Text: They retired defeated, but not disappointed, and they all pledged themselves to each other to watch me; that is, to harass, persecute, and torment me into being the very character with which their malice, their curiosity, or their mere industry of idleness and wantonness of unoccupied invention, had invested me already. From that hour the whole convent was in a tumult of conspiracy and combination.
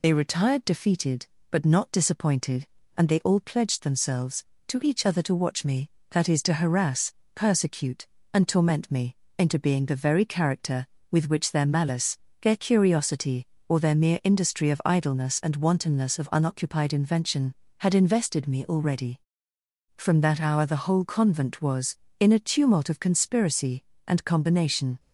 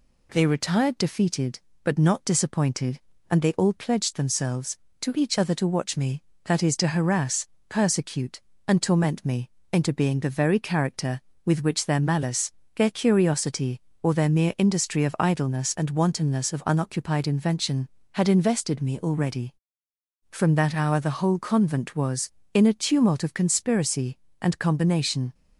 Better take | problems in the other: second | loses the start of "They"; at 0.0 s; 65 ms // pauses between "me" and "into"; slight; at 9.1 s; 0.24 s long; slight in the second

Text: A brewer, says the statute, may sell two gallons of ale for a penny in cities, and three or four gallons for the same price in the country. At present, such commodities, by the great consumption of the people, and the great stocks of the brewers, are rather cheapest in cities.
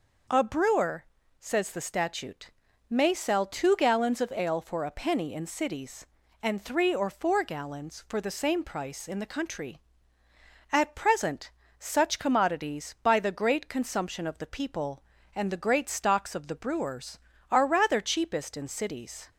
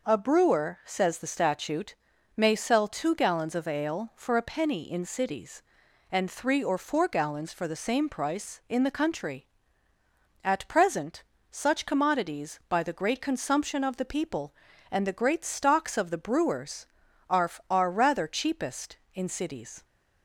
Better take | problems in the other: first | says "are" twice; at 17.7 s

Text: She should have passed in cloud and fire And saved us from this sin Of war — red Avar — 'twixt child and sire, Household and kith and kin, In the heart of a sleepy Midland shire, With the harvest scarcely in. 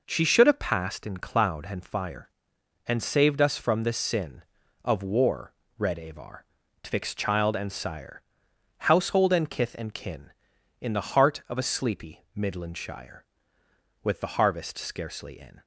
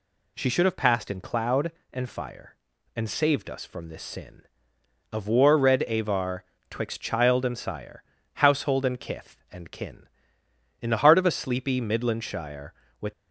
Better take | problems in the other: first | stops before "the harvest scarcely in"; at 13.1 s

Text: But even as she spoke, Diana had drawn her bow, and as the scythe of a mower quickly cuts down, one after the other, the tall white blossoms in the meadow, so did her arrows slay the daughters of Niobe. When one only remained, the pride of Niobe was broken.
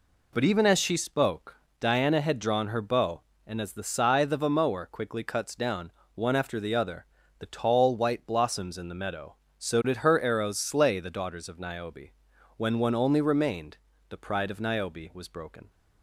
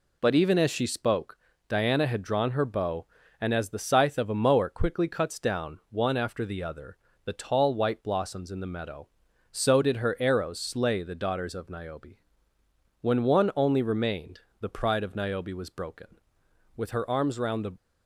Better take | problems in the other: first | goes on to say "With her arms round the"; noticeable; from 16.7 s on; 0.98 s long

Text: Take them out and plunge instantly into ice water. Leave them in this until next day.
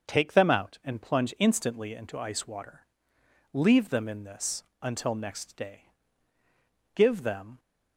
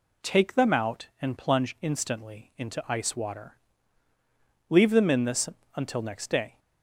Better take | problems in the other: second | starts louder than the rest; until 1.1 s; 6.5 dB // pauses between "this" and "until"; slight; at 4.6 s; 0.18 s long; slight in the second // goes on to say "Give them"; noticeable; from 6.9 s on; 0.64 s long

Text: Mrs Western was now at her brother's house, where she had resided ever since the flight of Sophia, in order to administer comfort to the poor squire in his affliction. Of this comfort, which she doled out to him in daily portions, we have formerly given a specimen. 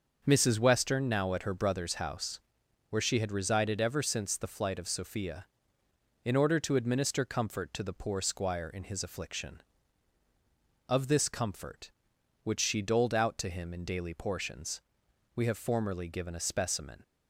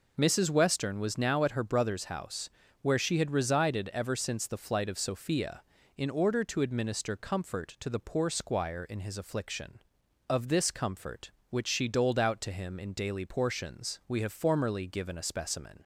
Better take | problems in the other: second | starts louder than the rest; until 1.2 s; 6.5 dB // skips "was"; at 1.0 s

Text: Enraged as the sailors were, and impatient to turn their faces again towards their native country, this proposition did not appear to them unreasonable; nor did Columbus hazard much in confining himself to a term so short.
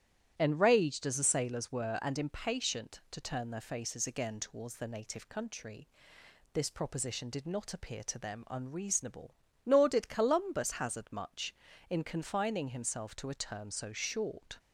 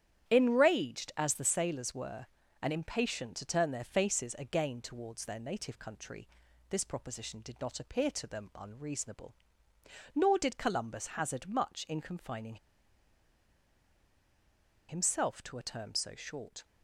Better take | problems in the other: first | starts louder than the rest; strong; until 1.3 s; 10 dB; strong in the first // pauses between "confining" and "himself"; strong; at 12.5 s; 2.3 s long

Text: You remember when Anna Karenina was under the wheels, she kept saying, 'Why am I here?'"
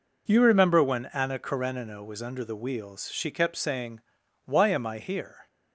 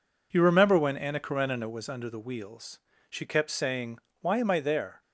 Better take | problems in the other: first | says "there" for "here"; at 4.6 s

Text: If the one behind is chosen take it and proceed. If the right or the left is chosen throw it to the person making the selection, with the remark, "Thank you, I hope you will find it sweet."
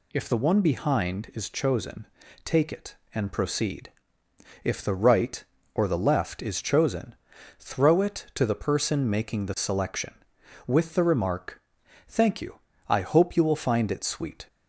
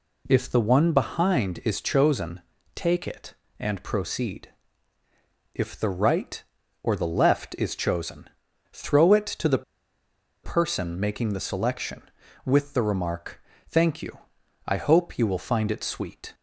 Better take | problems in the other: first | pauses between "chosen" and "take"; slight; at 2.4 s; 0.34 s long; also in the first // pauses between "chosen" and "throw"; at 8.2 s; 0.44 s long; also in the first // pauses between "the" and "person"; noticeable; at 9.6 s; 0.79 s long

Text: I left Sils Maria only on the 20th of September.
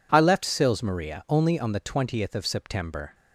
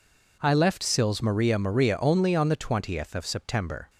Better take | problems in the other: first | says "Maria" twice; at 1.5 s

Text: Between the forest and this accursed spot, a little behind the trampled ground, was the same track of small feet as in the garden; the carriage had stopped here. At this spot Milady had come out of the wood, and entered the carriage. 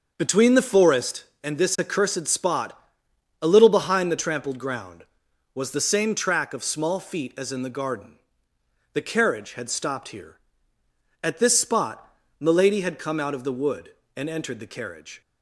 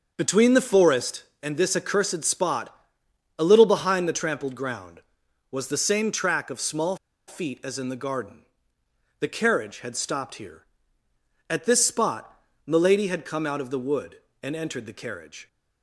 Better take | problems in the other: first | starts louder than the rest; noticeable; until 1.1 s; 6 dB // pauses between "small" and "feet"; slight; at 6.9 s; 0.32 s long // pauses between "spot" and "Milady"; slight; at 12.4 s; 0.24 s long; slight in the first

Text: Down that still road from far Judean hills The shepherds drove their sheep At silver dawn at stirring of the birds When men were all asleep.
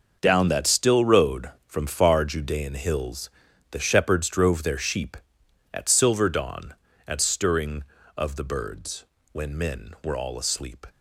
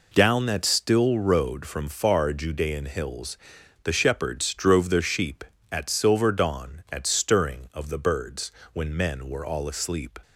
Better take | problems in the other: second | gets quieter; strong; throughout; 11.5 dB // pauses between "hills" and "The"; at 3.2 s; 0.42 s long; noticeable in the second // pauses between "birds" and "When"; slight; at 9.0 s; 0.28 s long; slight in the second

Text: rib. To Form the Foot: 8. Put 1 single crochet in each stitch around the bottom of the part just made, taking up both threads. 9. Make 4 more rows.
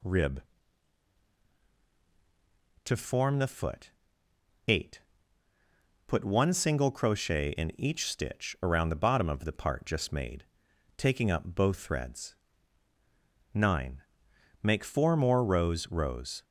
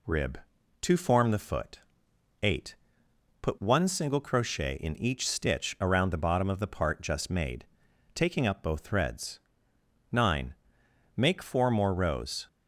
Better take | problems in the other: second | says "rows" twice; at 15.8 s

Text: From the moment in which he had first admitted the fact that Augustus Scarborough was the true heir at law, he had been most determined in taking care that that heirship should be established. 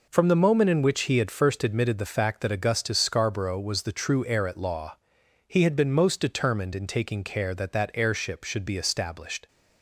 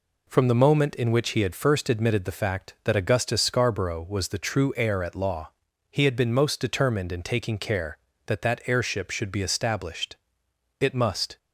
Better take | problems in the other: first | goes on to say "It must"; from 10.7 s on; 0.58 s long

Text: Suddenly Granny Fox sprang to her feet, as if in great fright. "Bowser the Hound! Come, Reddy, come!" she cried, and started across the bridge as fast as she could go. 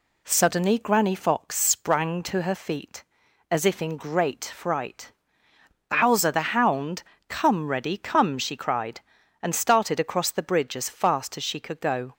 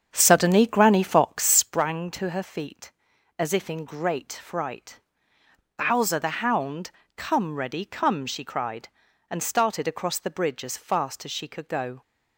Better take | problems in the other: first | starts louder than the rest; strong; until 1.9 s; 7.5 dB

